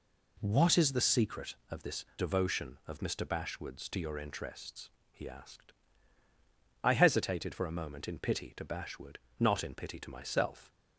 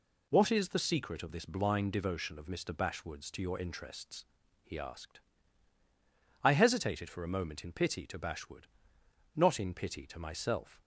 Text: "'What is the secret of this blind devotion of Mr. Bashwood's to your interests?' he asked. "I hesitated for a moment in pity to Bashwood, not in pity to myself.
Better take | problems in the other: second | skips "blind"; at 2.1 s

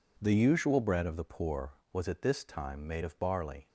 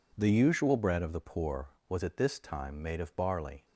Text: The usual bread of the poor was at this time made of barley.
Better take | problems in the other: neither | none

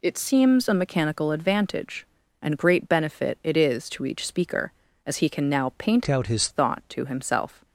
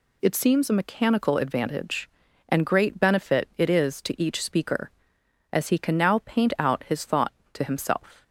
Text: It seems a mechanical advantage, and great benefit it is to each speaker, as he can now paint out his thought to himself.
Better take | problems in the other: second | changes voice from "out" to "his"; from 6.0 to 6.4 s; 0.4 s long

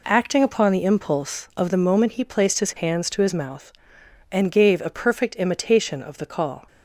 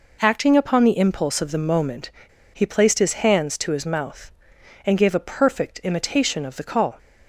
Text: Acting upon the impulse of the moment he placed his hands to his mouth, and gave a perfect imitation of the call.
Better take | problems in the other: first | pauses between "moment" and "he"; at 2.1 s; 0.43 s long

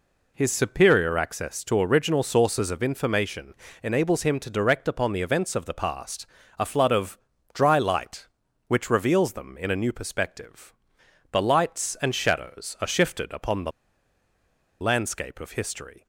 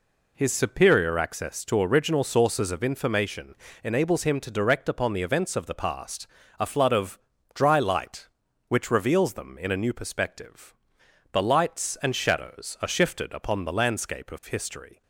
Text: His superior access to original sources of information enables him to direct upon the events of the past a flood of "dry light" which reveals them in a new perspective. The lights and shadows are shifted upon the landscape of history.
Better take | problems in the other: second | pauses between "information" and "enables"; slight; at 3.5 s; 0.28 s long; slight in the second // pauses between "past" and "a"; slight; at 6.2 s; 0.34 s long; slight in the second // pauses between "of" and "dry"; slight; at 7.1 s; 0.36 s long; slight in the second // pauses between "the" and "landscape"; at 13.7 s; 1.0 s long

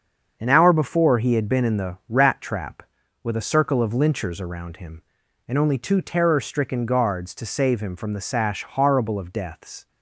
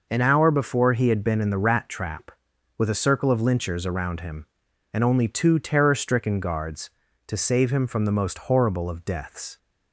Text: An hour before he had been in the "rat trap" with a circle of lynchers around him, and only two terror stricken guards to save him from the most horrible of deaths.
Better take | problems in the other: second | starts louder than the rest; until 1.4 s; 7 dB // says "sash" for "most"; at 8.2 s

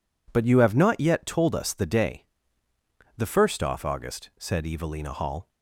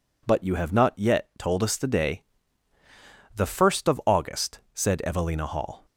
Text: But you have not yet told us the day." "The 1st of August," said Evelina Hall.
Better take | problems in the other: second | says "off" for "of"; at 3.6 s

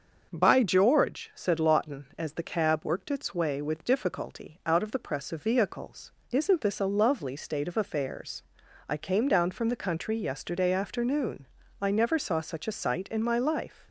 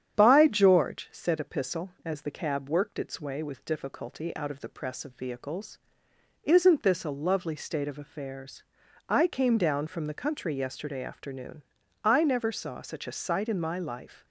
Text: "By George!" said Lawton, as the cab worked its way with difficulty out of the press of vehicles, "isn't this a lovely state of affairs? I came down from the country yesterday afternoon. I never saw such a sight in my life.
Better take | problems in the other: first | starts louder than the rest; strong; until 1.1 s; 9 dB; also in the first // says "Epistle" for "Lawton"; at 1.3 s

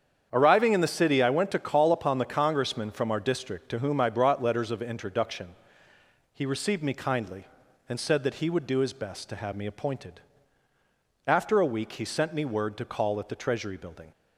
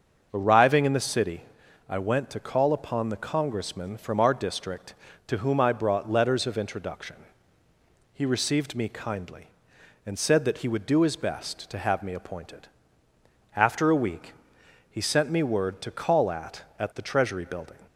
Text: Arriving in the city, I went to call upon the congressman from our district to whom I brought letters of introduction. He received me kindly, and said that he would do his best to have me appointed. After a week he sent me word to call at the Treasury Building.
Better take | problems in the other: first | starts louder than the rest; until 1.3 s; 6.5 dB; strong in the first // pauses between "week" and "he"; noticeable; at 14.3 s; 0.58 s long // says "at" twice; at 16.7 s

